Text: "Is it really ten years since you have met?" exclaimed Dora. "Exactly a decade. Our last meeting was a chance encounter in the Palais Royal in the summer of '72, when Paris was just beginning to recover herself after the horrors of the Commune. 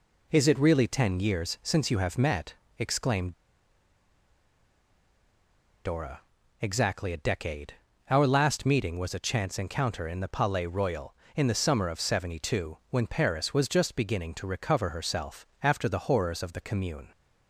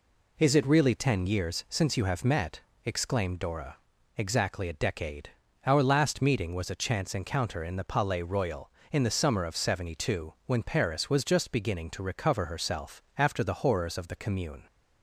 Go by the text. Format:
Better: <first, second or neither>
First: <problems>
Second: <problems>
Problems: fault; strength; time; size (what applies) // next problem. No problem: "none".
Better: second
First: pauses between "exclaimed" and "Dora"; strong; at 3.3 s; 2.5 s long // pauses between "herself" and "after"; slight; at 15.4 s; 0.16 s long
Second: none